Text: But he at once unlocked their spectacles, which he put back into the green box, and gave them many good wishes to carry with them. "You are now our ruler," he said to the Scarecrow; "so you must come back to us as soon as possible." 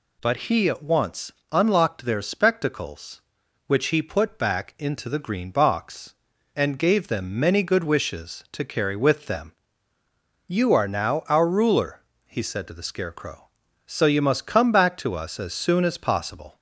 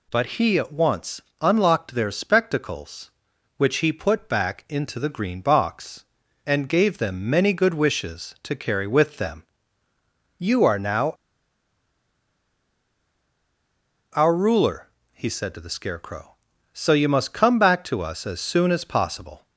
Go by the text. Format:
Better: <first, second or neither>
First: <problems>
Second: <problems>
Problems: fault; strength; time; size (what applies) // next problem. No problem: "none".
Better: first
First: pauses between "once" and "unlocked"; slight; at 1.3 s; 0.20 s long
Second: pauses between "once" and "unlocked"; slight; at 1.2 s; 0.20 s long // pauses between "now" and "our"; strong; at 11.1 s; 3.0 s long